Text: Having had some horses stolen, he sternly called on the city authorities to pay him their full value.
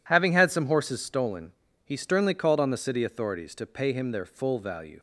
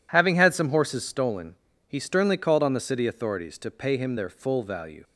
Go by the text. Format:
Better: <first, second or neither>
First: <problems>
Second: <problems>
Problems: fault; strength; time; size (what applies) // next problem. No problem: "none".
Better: neither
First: none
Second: none